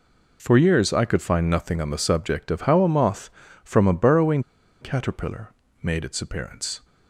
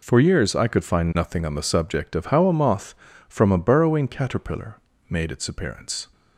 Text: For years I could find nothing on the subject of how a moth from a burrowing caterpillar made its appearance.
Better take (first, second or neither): second